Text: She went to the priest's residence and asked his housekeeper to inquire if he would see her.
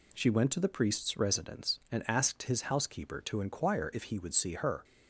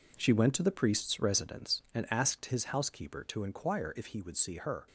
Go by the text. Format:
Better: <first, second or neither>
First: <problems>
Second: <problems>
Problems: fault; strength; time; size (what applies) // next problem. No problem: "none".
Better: first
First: none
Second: gets quieter; strong; throughout; 9 dB